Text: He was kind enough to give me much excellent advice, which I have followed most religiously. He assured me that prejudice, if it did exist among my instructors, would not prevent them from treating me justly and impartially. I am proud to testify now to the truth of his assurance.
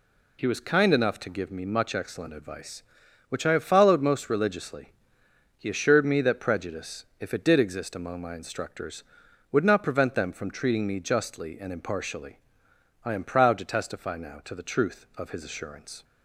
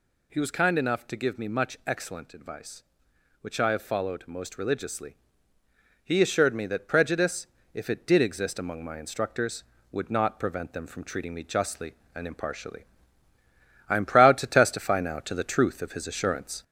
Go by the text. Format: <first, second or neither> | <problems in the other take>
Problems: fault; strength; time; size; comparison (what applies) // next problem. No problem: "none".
first | gets louder; slight; throughout; 3 dB